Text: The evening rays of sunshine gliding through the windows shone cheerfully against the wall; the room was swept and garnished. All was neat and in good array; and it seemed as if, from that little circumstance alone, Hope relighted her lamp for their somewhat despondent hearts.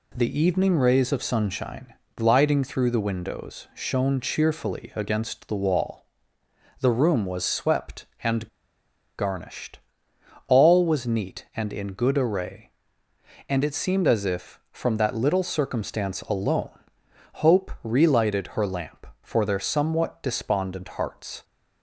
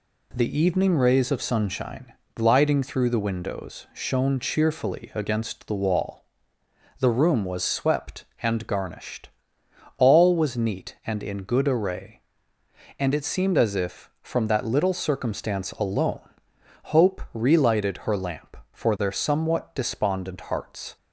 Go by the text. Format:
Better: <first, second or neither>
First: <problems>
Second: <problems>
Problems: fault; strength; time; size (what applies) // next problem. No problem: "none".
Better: second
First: pauses between "sunshine" and "gliding"; slight; at 1.9 s; 0.22 s long // pauses between "and" and "garnished"; noticeable; at 8.4 s; 0.71 s long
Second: pauses between "sunshine" and "gliding"; slight; at 2.1 s; 0.22 s long